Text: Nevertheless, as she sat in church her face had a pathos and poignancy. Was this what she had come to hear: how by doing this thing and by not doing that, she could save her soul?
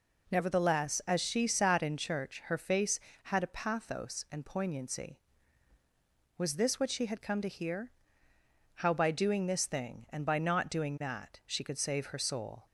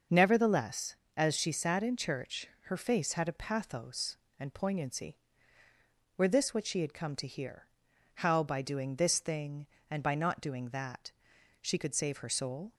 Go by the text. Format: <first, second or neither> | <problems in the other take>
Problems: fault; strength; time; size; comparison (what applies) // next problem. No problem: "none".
first | starts louder than the rest; noticeable; until 1.3 s; 6 dB // pauses between "church" and "her"; slight; at 2.4 s; 0.20 s long // says "Were" for "Was"; at 6.1 s